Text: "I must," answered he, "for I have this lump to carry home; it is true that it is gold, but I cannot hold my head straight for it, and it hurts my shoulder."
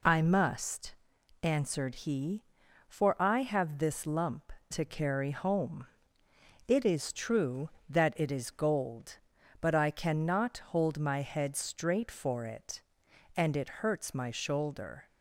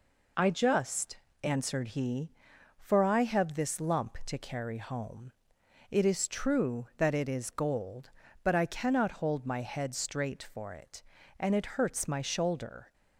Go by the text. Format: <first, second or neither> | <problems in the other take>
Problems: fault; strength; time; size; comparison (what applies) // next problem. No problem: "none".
first | says "just" for "must"; at 0.4 s